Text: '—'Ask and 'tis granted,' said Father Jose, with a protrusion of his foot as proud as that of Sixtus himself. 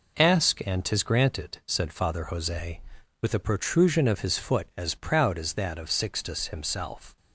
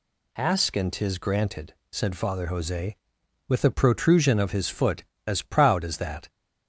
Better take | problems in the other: first | stops before "of Sixtus himself"; at 6.2 s

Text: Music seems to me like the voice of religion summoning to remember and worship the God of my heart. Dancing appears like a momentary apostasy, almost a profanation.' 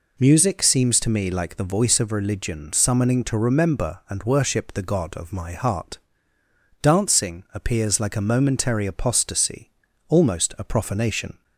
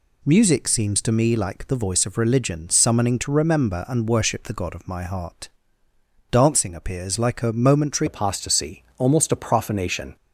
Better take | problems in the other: first | changes voice at "apostasy"; from 8.0 s on; 2.1 s long

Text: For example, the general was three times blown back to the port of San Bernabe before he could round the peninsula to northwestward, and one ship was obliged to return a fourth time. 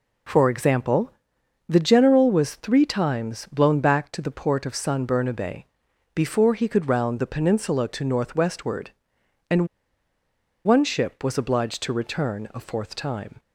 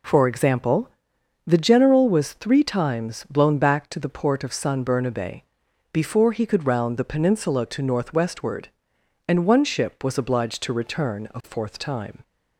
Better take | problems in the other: second | pauses between "Bernabe" and "before"; noticeable; at 5.6 s; 0.52 s long; noticeable in the second // pauses between "and" and "one"; at 9.6 s; 0.99 s long

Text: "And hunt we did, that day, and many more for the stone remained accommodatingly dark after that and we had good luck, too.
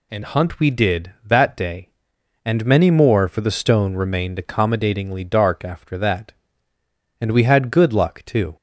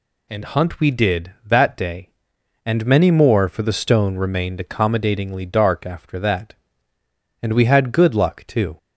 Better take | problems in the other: neither | none

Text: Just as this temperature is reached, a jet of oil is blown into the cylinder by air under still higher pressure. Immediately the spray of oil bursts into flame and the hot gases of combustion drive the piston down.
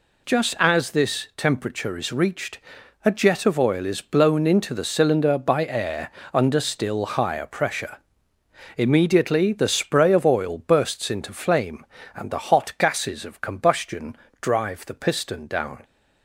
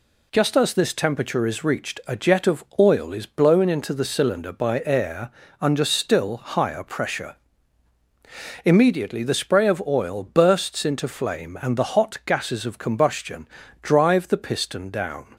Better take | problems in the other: neither | pauses between "air" and "under"; slight; the same in both // pauses between "combustion" and "drive"; slight; the same in both

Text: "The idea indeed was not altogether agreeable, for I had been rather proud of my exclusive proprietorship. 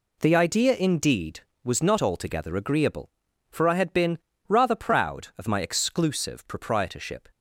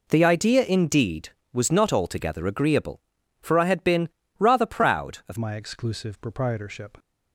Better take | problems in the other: first | pauses between "been" and "rather"; slight; at 4.0 s; 0.28 s long; slight in the first // changes voice at "my"; from 5.3 s on; 1.6 s long

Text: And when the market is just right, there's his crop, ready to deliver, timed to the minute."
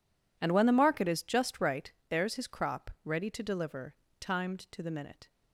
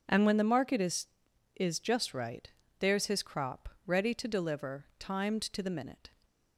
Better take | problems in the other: first | says "is" twice; at 1.5 s

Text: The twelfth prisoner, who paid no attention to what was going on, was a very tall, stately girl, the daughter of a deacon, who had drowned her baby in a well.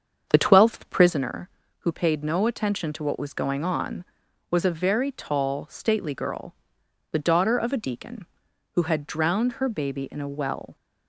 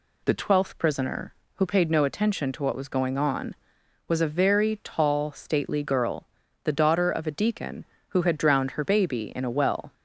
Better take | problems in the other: second | starts louder than the rest; strong; until 1.2 s; 7 dB

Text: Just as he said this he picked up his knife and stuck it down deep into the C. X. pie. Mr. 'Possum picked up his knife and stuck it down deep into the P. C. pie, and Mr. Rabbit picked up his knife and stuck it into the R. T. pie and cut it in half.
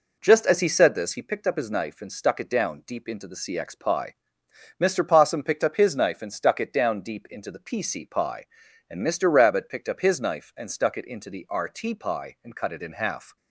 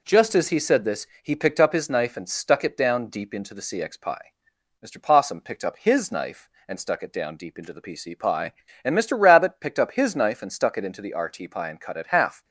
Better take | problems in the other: first | pauses between "this" and "he"; slight; at 1.0 s; 0.16 s long // skips "in"; at 12.0 s

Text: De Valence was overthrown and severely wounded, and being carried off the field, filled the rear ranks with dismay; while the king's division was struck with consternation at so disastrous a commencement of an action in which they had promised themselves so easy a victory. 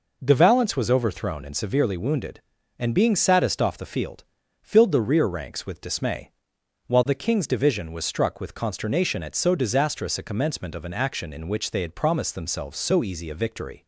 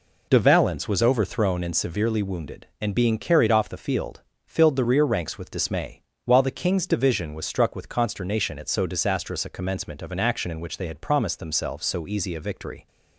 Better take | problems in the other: second | says "saddest" for "carried"; at 3.1 s

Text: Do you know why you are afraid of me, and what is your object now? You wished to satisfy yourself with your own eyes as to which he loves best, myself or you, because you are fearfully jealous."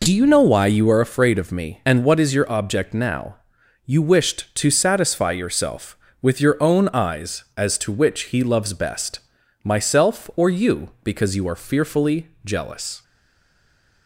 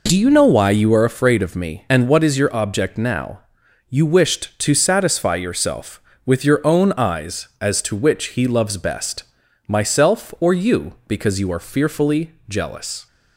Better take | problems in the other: second | pauses between "fearfully" and "jealous"; slight; at 12.2 s; 0.16 s long; slight in the second // stays silent after the last word; from 13.0 s on; 1.0 s long

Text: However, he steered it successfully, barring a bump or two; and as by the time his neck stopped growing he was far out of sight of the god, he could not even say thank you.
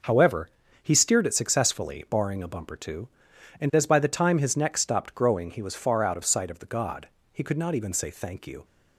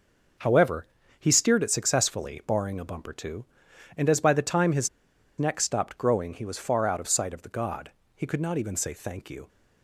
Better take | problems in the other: first | starts louder than the rest; noticeable; until 1.7 s; 6 dB; noticeable in the first // pauses between "his" and "neck"; noticeable; at 4.8 s; 0.49 s long

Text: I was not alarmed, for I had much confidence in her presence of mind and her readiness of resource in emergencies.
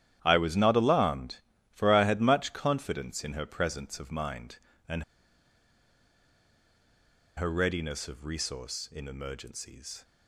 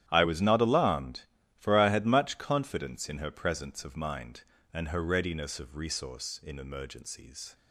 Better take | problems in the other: second | starts louder than the rest; strong; until 1.2 s; 11 dB; strong in the second // pauses between "and" and "her"; strong; at 5.0 s; 2.3 s long

